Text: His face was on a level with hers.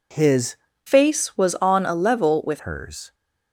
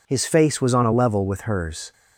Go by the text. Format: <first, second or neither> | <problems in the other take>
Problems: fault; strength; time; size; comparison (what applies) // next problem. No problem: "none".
second | changes voice from "face" to "with"; from 0.8 to 2.6 s; 1.8 s long